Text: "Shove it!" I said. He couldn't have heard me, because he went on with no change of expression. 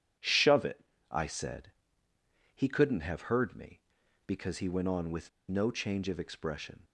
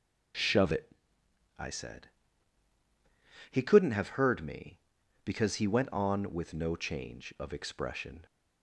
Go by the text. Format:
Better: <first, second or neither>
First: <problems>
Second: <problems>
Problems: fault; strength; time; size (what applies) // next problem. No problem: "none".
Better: second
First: pauses between "with" and "no"; slight; at 5.2 s; 0.18 s long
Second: none